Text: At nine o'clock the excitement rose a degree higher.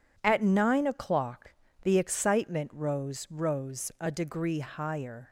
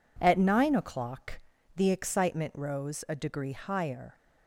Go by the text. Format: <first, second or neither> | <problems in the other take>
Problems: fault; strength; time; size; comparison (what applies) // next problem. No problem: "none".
second | pauses between "o'clock" and "the"; slight; at 1.5 s; 0.32 s long; slight in the second // says "rose" twice; at 3.2 s